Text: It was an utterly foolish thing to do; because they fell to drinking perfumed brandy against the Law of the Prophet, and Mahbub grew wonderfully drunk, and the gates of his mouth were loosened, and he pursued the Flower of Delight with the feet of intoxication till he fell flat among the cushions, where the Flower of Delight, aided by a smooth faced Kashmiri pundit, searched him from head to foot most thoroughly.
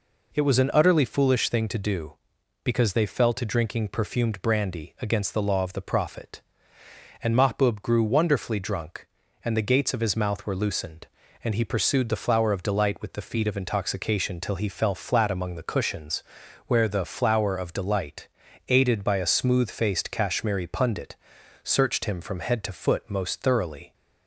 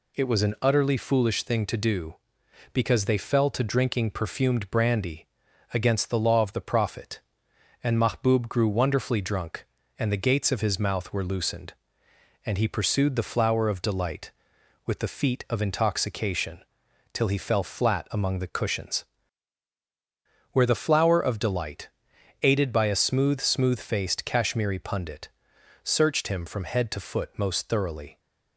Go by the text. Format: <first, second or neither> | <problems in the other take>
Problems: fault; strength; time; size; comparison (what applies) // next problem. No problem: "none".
first | pauses between "brandy" and "against"; at 5.2 s; 0.44 s long // pauses between "intoxication" and "till"; noticeable; at 16.6 s; 0.50 s long // says "smooth" twice; at 23.3 s